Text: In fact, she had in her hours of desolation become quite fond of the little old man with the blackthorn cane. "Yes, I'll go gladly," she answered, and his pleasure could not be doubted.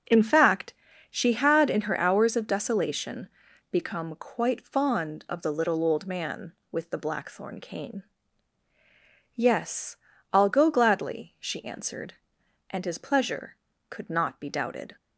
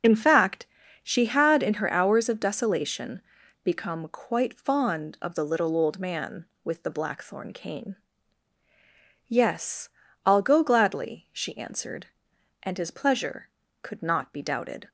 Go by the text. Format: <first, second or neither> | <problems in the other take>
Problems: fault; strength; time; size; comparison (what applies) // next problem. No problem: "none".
first | loses the start of "In"; at 0.0 s; 45 ms // starts louder than the rest; until 1.4 s; 6.5 dB; noticeable in the first // pauses between "desolation" and "become"; at 3.2 s; 0.42 s long; also in the first